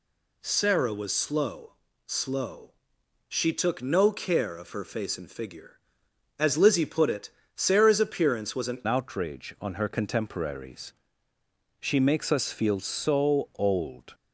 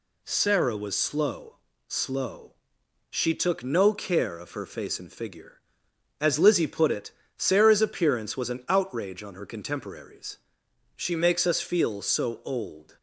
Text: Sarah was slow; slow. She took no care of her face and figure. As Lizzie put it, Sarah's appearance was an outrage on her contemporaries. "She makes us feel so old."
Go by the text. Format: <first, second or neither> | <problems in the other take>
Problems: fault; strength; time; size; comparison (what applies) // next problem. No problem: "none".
second | changes voice at "outrage"; from 8.8 s on; 5.3 s long